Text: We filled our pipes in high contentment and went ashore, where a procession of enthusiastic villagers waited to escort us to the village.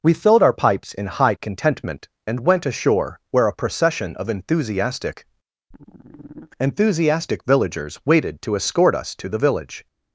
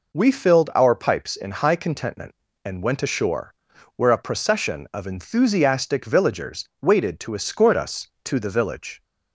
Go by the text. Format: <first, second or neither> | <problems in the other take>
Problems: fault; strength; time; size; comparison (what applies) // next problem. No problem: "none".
second | says "enthusiastic" twice; at 6.5 s